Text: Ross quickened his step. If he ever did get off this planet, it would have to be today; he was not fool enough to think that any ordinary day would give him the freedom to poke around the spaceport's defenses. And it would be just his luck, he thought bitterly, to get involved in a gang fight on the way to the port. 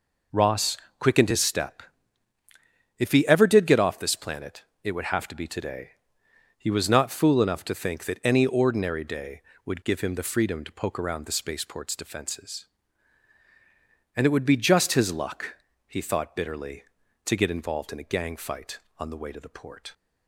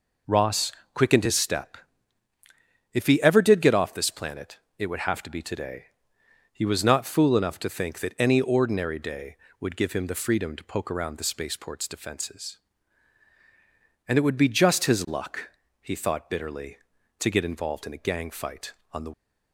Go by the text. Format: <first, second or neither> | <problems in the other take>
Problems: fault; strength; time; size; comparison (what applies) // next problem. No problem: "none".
first | pauses between "Ross" and "quickened"; slight; at 0.7 s; 0.22 s long; slight in the first // stops before "way to the port"; at 19.1 s